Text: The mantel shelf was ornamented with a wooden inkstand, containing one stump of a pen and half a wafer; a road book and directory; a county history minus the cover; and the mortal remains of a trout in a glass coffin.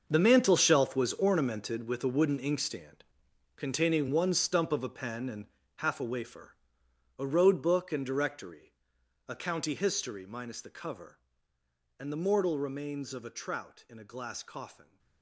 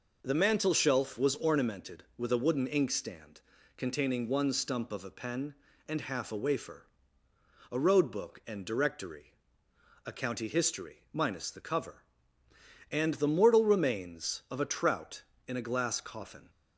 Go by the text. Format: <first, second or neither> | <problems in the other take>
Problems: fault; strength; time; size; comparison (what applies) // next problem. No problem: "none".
second | gets quieter; strong; throughout; 14 dB // pauses between "and" and "half"; slight; at 5.4 s; 0.30 s long